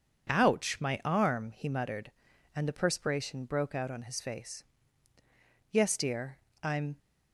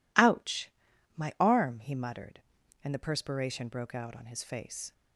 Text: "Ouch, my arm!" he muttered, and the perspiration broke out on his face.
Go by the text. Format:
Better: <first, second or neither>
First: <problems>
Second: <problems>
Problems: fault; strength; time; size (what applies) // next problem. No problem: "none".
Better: second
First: goes on to say "Yes dear I'm"; noticeable; from 5.6 s on; 1.2 s long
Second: none